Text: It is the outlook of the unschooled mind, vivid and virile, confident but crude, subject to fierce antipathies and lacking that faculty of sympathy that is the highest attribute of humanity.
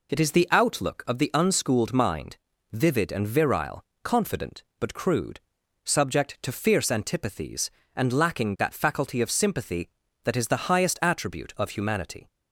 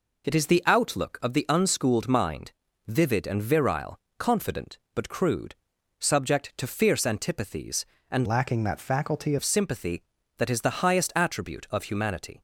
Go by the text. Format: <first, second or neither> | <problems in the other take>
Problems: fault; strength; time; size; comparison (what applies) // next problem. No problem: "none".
first | changes voice from "lacking" to "faculty"; from 8.2 to 9.3 s; 1.1 s long